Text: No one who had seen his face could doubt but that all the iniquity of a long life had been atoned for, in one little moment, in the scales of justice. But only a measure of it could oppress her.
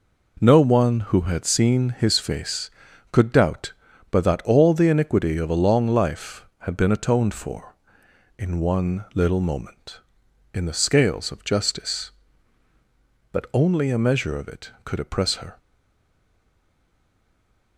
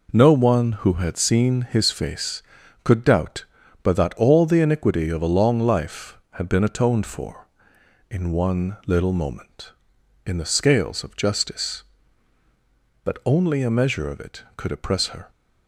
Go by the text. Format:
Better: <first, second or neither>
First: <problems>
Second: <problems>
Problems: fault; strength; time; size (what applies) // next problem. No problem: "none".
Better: second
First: stays silent after the last word; from 15.5 s on; 2.2 s long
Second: none